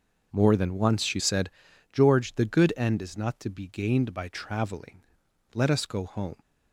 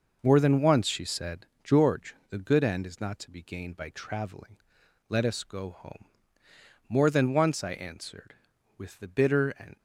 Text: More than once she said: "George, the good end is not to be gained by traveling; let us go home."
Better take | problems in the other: first | goes on to say "More than once I answered with the bitter and"; strong; from 6.8 s on; 2.8 s long

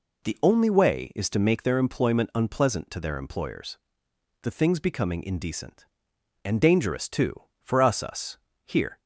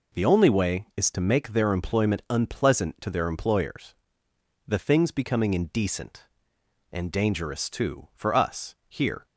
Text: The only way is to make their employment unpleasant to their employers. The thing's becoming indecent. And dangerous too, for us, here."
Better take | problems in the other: second | says "us" twice; at 8.0 s

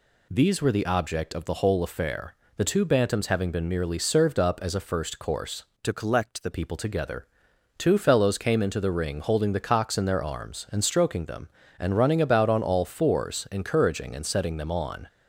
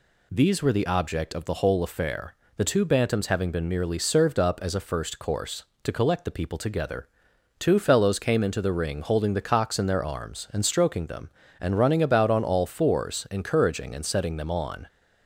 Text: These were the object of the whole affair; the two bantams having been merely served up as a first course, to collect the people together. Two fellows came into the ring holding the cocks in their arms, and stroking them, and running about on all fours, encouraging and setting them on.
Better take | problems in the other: second | changes voice from "to" to "the"; from 5.8 to 6.4 s; 0.6 s long

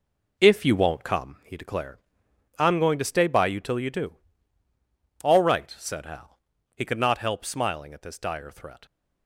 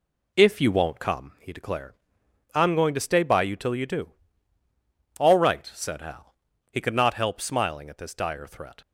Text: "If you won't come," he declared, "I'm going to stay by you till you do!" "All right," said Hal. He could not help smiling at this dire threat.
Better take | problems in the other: second | gets quieter; strong; throughout; 8 dB

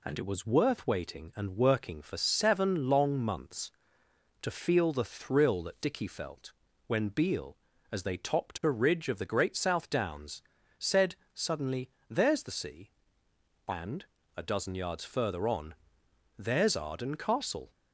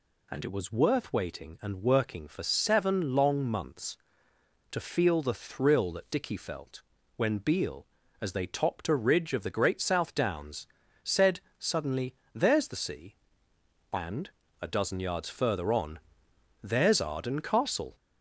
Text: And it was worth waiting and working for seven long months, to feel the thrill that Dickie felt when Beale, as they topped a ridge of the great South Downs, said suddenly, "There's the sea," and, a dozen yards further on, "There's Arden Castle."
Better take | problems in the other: first | gets louder; slight; throughout; 3 dB // pauses between "felt" and "when"; slight; at 6.8 s; 0.36 s long; slight in the first // pauses between "said" and "suddenly"; slight; at 11.4 s; 0.18 s long; slight in the first

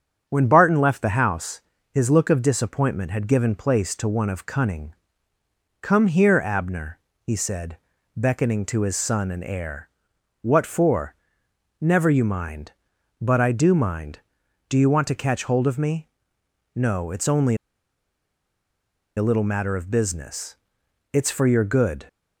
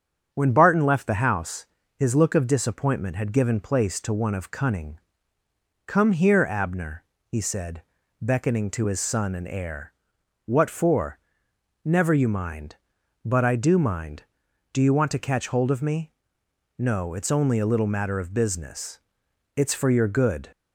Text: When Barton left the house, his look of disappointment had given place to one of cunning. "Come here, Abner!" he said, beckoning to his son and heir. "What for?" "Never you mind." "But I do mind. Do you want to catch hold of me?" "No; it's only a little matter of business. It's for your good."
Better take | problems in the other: second | starts louder than the rest; strong; until 1.2 s; 7.5 dB; strong in the second // pauses between "only" and "a"; strong; at 17.5 s; 1.6 s long

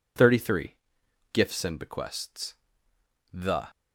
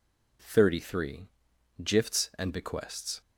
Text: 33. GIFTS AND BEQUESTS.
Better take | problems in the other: second | goes on to say "The"; slight; from 3.3 s on; 0.36 s long

